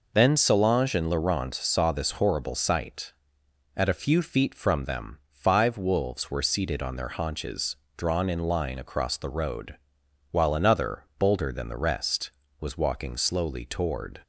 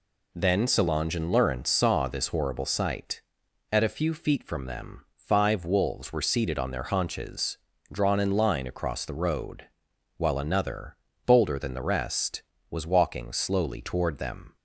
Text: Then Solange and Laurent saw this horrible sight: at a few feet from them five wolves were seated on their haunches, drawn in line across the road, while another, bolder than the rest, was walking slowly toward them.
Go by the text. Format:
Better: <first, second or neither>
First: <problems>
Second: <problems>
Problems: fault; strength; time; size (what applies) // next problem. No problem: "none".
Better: second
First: stops before "them"; at 14.2 s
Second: none